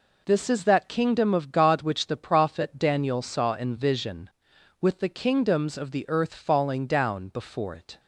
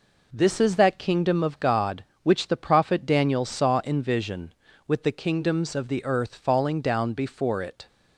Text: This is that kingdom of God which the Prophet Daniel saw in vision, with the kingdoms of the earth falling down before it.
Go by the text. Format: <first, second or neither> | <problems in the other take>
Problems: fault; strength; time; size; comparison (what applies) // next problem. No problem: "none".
neither | none